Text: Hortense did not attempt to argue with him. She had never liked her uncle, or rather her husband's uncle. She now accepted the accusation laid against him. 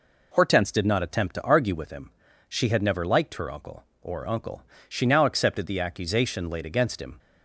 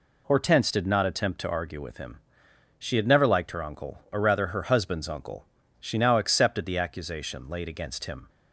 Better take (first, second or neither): second